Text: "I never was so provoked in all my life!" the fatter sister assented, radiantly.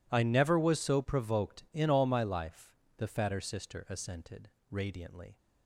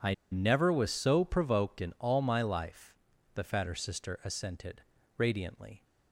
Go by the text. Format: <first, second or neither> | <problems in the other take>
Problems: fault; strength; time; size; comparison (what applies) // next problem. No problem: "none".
first | pauses between "I" and "never"; slight; at 0.1 s; 0.17 s long